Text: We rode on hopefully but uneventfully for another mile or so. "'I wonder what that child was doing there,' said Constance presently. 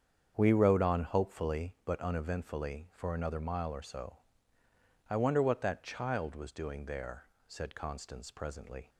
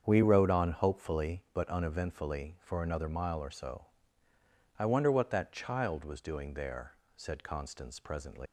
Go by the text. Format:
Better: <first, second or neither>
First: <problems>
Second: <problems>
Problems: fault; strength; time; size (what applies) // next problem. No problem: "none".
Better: first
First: starts louder than the rest; strong; until 1.3 s; 7.5 dB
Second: starts louder than the rest; strong; until 1.0 s; 7.5 dB // leaves "presently" unfinished; at 8.4 s; 115 ms